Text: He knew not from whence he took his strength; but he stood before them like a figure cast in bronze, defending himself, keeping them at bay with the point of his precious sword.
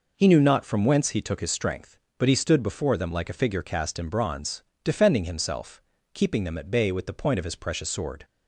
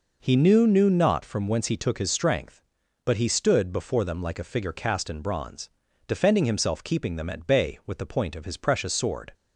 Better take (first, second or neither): first